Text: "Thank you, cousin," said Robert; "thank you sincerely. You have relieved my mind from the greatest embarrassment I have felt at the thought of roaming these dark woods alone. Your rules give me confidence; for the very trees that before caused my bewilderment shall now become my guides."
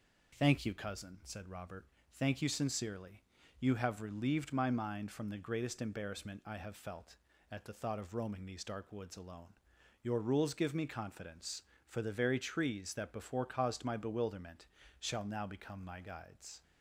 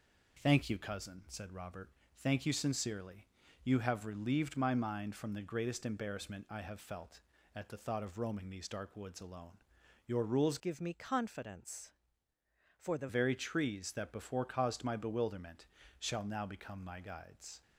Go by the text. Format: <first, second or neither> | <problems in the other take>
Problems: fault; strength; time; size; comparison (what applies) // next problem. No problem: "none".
first | changes voice from "give" to "the"; from 10.5 to 13.0 s; 2.5 s long // pauses between "bewilderment" and "shall"; slight; at 15.6 s; 0.32 s long; slight in the first